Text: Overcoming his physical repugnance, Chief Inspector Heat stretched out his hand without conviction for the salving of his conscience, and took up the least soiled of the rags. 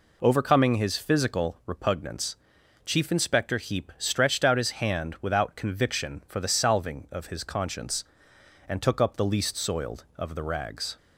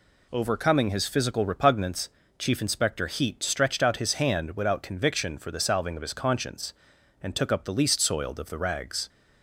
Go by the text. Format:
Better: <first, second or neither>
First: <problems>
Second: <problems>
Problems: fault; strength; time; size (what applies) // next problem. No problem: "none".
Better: second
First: says "Heap" for "Heat"; at 3.5 s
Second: none